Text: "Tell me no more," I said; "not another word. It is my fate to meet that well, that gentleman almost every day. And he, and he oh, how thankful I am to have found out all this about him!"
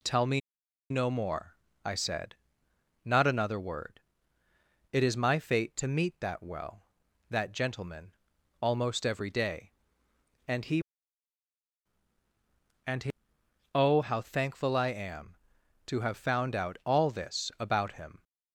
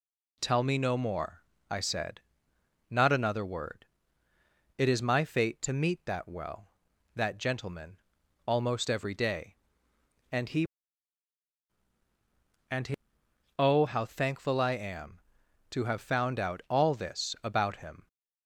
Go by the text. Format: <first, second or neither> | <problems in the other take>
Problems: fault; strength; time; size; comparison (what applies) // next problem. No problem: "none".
second | pauses between "me" and "no"; noticeable; at 0.4 s; 0.50 s long // pauses between "gentleman" and "almost"; noticeable; at 8.1 s; 0.46 s long; noticeable in the second // pauses between "he" and "oh"; noticeable; at 13.1 s; 0.64 s long; noticeable in the second